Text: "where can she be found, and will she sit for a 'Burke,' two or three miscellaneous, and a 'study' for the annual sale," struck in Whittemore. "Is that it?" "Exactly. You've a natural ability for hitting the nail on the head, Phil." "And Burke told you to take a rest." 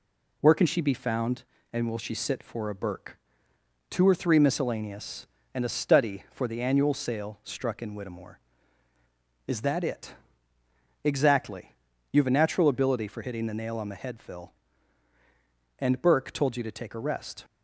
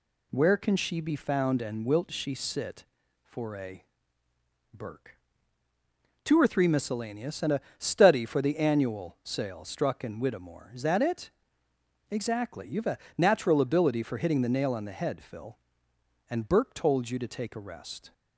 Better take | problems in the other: first | says "wilt" for "will"; at 1.8 s // pauses between "a" and "Burke"; noticeable; at 3.8 s; 0.88 s long // pauses between "a" and "study"; slight; at 7.6 s; 0.18 s long // pauses between "a" and "natural"; slight; at 12.9 s; 0.20 s long

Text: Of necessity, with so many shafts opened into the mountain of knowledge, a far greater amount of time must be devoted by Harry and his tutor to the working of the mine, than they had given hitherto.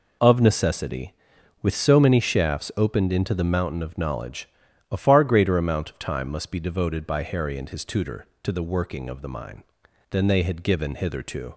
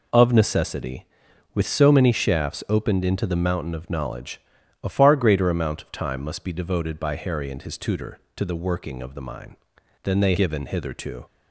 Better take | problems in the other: first | skips "had"; at 10.3 s

